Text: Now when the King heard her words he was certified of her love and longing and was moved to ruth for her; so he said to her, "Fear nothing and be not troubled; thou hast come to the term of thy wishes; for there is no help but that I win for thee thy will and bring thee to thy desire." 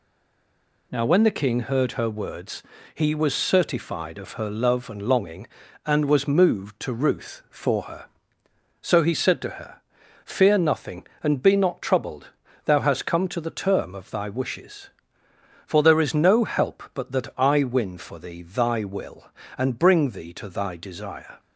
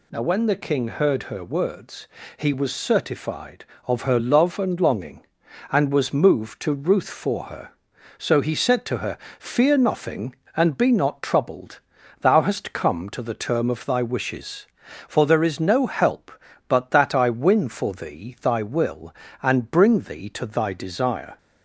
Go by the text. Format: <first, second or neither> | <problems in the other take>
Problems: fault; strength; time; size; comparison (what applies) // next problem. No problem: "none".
second | stays silent before the first word; slight; until 0.9 s; 0.9 s long // pauses between "words" and "he"; slight; at 2.6 s; 0.32 s long; slight in the second